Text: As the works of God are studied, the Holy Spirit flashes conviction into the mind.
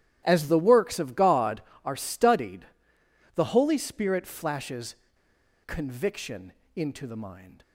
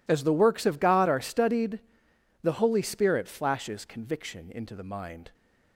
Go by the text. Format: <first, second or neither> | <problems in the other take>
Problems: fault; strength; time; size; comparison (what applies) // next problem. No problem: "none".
second | starts louder than the rest; strong; until 1.2 s; 13 dB // pauses between "flashes" and "conviction"; noticeable; at 4.9 s; 0.70 s long // pauses between "conviction" and "into"; slight; at 6.5 s; 0.22 s long